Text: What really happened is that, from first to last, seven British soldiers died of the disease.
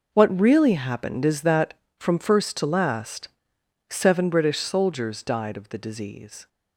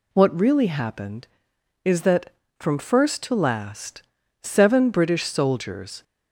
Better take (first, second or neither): first